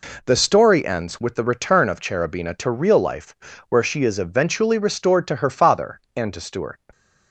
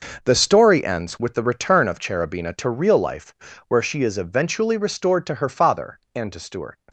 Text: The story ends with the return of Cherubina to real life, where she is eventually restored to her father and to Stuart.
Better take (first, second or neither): first